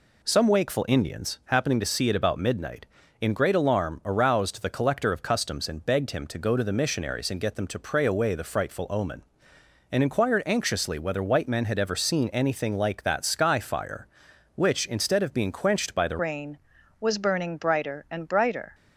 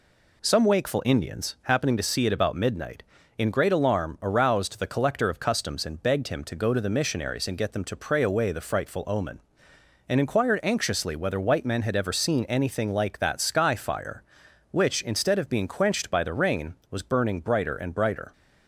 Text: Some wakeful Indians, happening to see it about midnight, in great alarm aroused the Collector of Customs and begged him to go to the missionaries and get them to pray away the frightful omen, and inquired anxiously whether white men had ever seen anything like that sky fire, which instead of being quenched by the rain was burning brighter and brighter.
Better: second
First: changes voice at "rain"; from 16.1 s on; 2.6 s long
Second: none

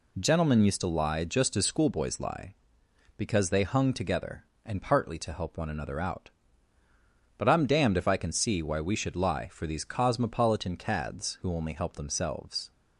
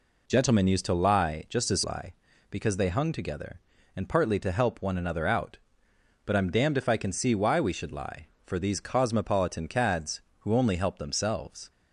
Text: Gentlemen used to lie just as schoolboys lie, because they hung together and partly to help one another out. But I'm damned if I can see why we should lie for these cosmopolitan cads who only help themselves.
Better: first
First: none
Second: skips "schoolboys"; at 1.8 s

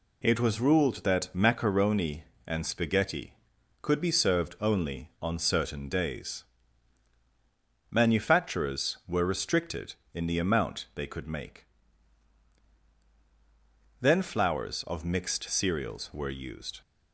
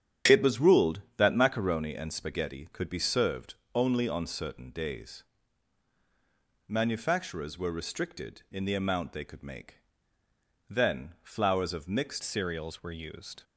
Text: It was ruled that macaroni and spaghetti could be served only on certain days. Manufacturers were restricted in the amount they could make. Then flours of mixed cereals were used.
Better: first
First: none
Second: starts louder than the rest; strong; until 1.4 s; 9.5 dB // pauses between "served" and "only"; slight; at 3.5 s; 0.22 s long // changes voice at "cereals"; from 12.2 s on; 1.2 s long

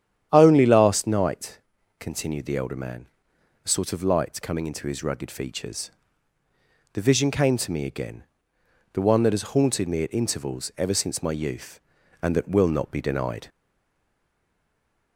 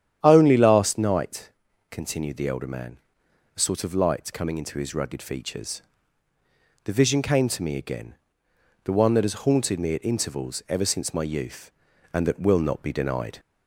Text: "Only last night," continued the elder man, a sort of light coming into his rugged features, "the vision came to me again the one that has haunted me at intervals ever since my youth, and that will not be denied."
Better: second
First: starts louder than the rest; strong; until 1.3 s; 9.5 dB // pauses between "again" and "the"; noticeable; at 8.2 s; 0.68 s long // stays silent after the last word; noticeable; from 13.4 s on; 1.7 s long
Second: starts louder than the rest; strong; until 1.2 s; 9.5 dB // pauses between "again" and "the"; noticeable; at 8.1 s; 0.68 s long

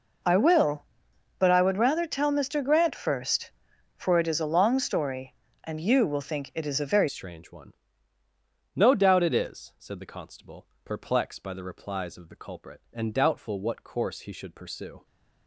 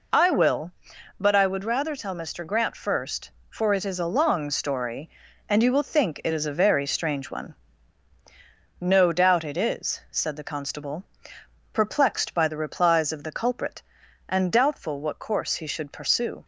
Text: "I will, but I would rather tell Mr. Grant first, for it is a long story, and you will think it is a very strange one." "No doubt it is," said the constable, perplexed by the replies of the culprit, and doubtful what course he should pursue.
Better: second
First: changes voice at "strange"; from 7.0 s on; 8.0 s long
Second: none

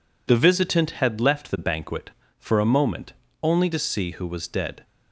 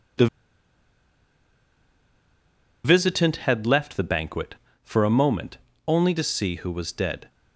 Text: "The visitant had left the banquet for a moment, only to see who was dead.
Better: first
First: none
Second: pauses between "The" and "visitant"; strong; at 0.2 s; 2.5 s long

